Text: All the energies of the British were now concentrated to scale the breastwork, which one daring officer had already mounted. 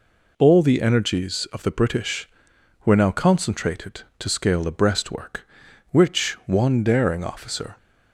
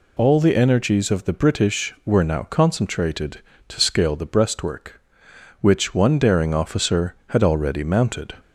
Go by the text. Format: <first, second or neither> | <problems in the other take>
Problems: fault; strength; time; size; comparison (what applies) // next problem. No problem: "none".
second | stops before "had already mounted"; at 7.7 s